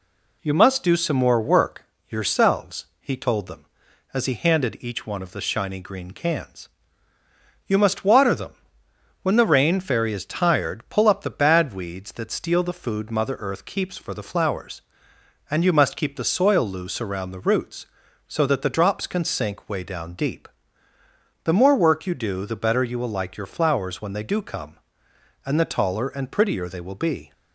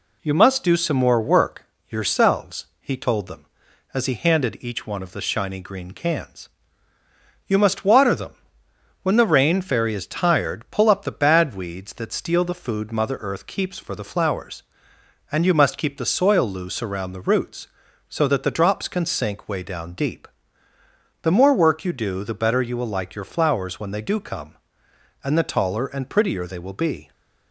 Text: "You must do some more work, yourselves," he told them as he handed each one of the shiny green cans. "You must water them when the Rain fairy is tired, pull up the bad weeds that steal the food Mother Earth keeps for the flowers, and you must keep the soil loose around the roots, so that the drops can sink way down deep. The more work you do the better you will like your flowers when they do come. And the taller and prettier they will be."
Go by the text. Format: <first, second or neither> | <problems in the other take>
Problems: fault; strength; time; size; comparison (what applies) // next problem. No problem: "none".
neither | pauses between "them" and "when"; noticeable; the same in both